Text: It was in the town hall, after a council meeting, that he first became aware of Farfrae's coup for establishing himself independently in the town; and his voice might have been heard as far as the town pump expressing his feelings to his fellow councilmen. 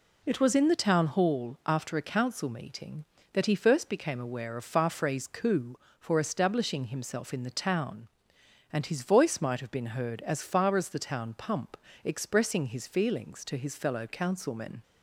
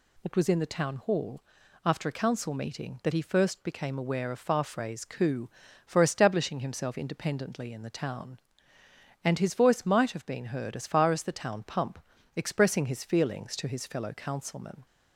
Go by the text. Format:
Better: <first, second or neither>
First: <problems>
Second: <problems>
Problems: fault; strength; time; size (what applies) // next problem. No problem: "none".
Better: second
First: skips "independently"; at 7.3 s // pauses between "pump" and "expressing"; slight; at 11.7 s; 0.28 s long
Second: pauses between "pump" and "expressing"; slight; at 11.9 s; 0.36 s long